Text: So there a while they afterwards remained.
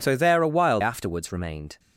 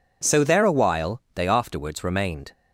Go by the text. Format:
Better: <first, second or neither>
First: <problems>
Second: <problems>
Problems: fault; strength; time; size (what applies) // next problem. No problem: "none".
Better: second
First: skips "they"; at 0.8 s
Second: none